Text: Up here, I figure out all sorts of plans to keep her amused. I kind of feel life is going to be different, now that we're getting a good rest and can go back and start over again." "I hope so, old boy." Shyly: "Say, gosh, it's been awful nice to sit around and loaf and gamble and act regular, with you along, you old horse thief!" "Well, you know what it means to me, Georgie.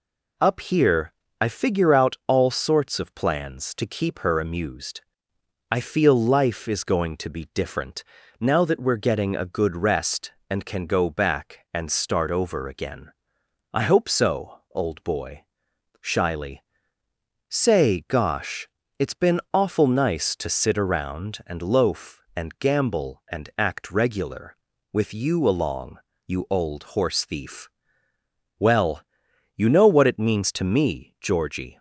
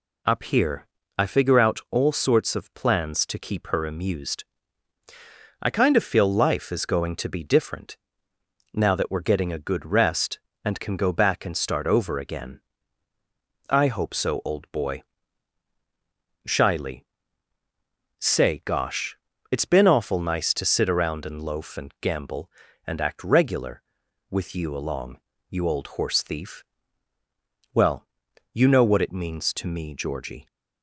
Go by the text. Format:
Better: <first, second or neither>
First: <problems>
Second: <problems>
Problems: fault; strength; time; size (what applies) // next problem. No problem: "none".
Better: second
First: skips "kind of"; at 5.8 s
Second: none